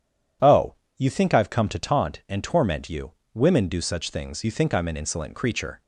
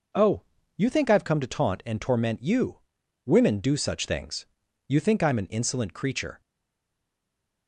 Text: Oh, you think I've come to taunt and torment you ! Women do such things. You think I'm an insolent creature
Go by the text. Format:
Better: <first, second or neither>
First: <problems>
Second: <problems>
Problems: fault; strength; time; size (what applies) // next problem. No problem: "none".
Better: first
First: none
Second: stays silent after the last word; noticeable; from 6.4 s on; 1.2 s long